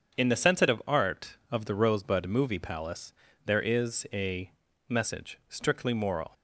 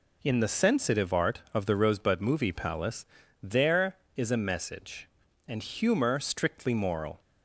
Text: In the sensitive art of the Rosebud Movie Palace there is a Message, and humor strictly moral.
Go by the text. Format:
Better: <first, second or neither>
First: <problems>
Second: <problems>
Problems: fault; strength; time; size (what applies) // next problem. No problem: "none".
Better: second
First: starts louder than the rest; until 1.1 s; 7 dB // pauses between "Palace" and "there"; slight; at 3.1 s; 0.34 s long // pauses between "a" and "Message"; slight; at 4.5 s; 0.36 s long // skips "and humor"; at 5.4 s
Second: pauses between "Palace" and "there"; slight; at 3.0 s; 0.36 s long